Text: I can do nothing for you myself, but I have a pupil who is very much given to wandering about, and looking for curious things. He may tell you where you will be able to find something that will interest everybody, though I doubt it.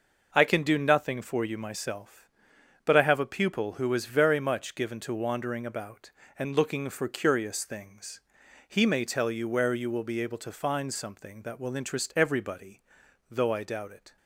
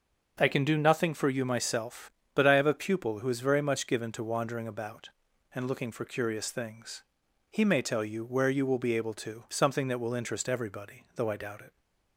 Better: first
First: none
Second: starts louder than the rest; until 1.4 s; 6.5 dB // skips "find"; at 9.4 s

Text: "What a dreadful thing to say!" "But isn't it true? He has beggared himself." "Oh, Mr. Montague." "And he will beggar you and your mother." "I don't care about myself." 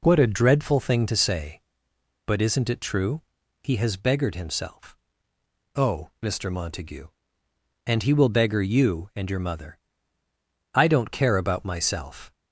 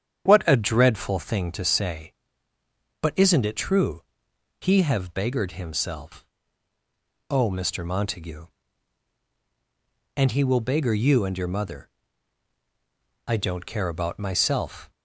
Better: first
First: none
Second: starts louder than the rest; strong; until 1.2 s; 9 dB // says "have" for "has"; at 4.8 s

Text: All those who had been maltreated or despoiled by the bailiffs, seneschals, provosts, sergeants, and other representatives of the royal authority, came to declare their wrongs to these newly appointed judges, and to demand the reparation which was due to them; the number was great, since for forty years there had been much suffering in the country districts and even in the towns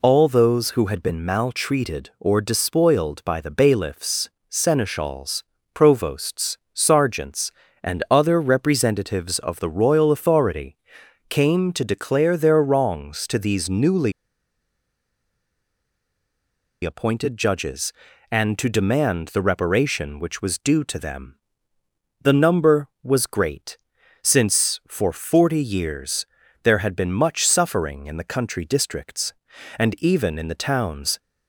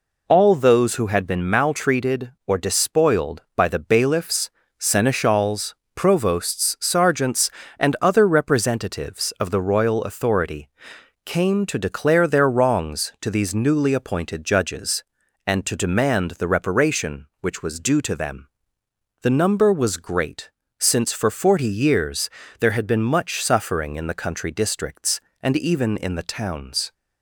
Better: second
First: pauses between "newly" and "appointed"; strong; at 14.1 s; 2.7 s long // pauses between "years" and "there"; at 26.2 s; 0.38 s long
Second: pauses between "years" and "there"; slight; at 22.2 s; 0.32 s long

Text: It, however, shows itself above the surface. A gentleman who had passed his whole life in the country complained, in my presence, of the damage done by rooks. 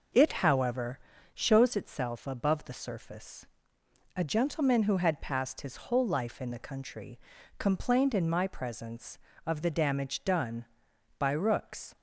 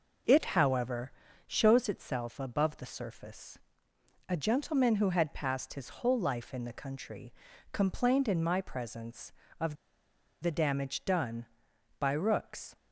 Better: first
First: pauses between "country" and "complained"; at 7.1 s; 0.40 s long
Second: pauses between "country" and "complained"; at 7.3 s; 0.40 s long // pauses between "of" and "the"; noticeable; at 9.7 s; 0.66 s long

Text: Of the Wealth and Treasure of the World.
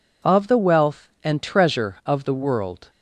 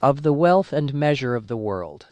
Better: first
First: none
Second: says "Measure" for "Treasure"; at 0.9 s

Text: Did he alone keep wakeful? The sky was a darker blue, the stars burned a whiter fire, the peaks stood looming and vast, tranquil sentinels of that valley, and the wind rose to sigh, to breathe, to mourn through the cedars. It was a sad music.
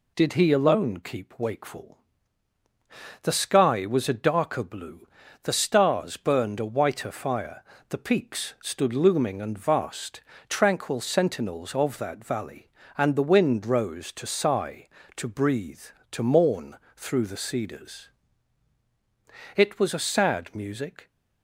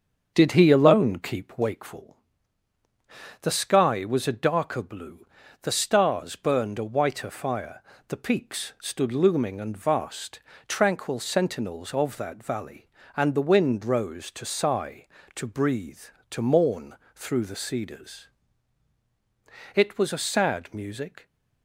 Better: first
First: pauses between "mourn" and "through"; slight; at 16.7 s; 0.18 s long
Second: starts louder than the rest; until 1.9 s; 7 dB // pauses between "mourn" and "through"; slight; at 16.9 s; 0.18 s long

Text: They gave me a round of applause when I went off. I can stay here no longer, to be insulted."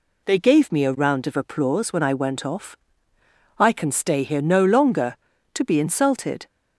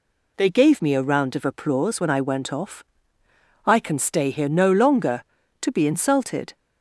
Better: neither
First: none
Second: none

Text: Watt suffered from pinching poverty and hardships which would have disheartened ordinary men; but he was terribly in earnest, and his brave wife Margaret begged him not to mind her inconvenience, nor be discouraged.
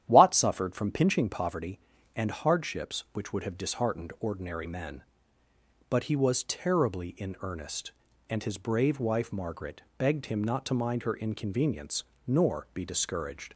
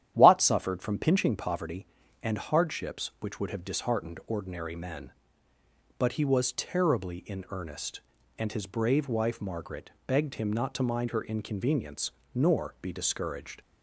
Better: neither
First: starts louder than the rest; strong; until 1.0 s; 10.5 dB // pauses between "Margaret" and "begged"; slight; at 9.8 s; 0.16 s long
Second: starts louder than the rest; strong; until 1.1 s; 10.5 dB // pauses between "Margaret" and "begged"; slight; at 9.9 s; 0.16 s long

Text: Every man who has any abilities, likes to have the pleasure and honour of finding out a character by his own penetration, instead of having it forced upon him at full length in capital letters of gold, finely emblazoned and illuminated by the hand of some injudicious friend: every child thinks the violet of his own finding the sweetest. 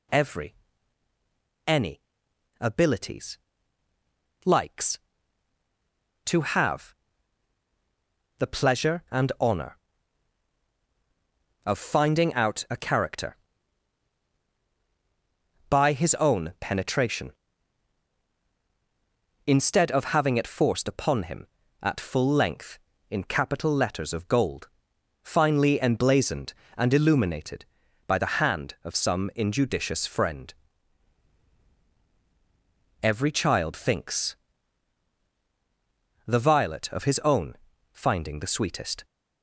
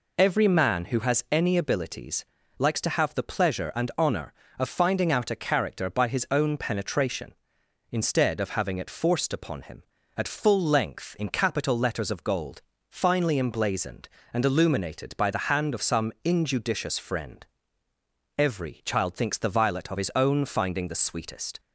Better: second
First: skips "man who has"; at 1.1 s // pauses between "any" and "abilities"; noticeable; at 2.0 s; 0.58 s long // pauses between "have" and "the"; strong; at 6.9 s; 1.4 s long // pauses between "thinks" and "the"; strong; at 34.3 s; 1.9 s long // pauses between "own" and "finding"; at 37.5 s; 0.38 s long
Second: none

